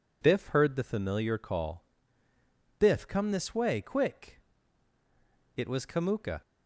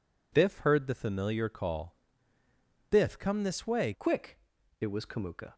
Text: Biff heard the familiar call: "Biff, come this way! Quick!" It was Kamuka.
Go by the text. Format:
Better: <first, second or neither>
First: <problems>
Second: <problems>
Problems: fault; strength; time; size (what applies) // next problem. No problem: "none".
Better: first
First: none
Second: changes voice at "Quick"; from 3.9 s on; 1.6 s long